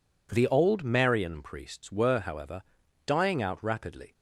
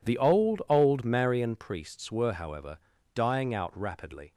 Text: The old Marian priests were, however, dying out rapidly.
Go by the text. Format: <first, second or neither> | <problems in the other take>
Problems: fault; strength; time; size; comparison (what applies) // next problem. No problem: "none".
first | says "old" twice; at 0.6 s